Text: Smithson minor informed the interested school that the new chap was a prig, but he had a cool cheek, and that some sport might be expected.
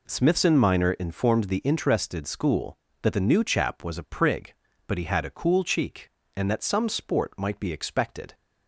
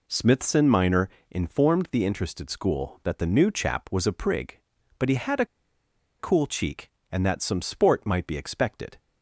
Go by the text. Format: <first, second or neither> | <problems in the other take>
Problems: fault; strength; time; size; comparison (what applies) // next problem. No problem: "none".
first | pauses between "minor" and "informed"; slight; at 1.0 s; 0.22 s long // pauses between "a" and "cool"; noticeable; at 5.4 s; 0.74 s long